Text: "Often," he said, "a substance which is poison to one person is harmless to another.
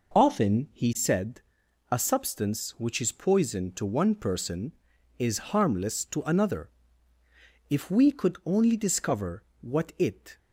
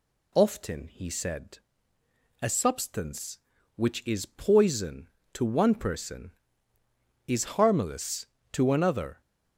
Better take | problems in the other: second | goes on to say "If we could only discover what it"; strong; from 7.6 s on; 2.7 s long

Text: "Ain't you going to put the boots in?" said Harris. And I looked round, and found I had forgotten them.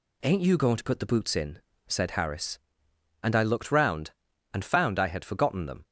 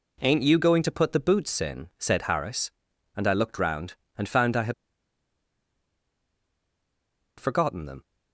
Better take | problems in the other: first | pauses between "had" and "forgotten"; strong; at 4.7 s; 2.6 s long

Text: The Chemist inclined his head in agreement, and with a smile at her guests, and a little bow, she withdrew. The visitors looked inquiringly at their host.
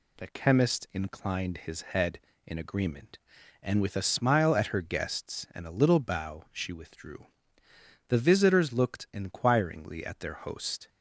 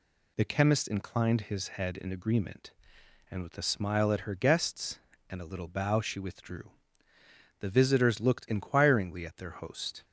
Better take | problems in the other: neither | none

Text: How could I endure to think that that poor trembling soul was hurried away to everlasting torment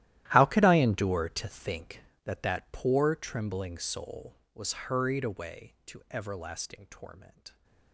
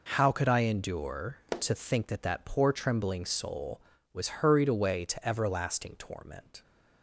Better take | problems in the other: second | gets quieter; strong; throughout; 17.5 dB

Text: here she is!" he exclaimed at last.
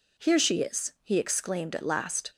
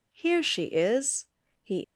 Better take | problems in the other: first | stops before "exclaimed at last"; at 1.8 s

